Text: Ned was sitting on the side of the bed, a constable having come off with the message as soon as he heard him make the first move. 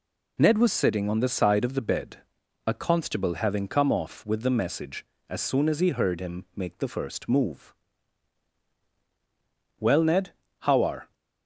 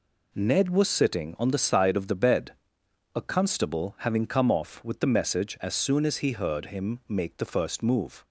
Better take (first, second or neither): second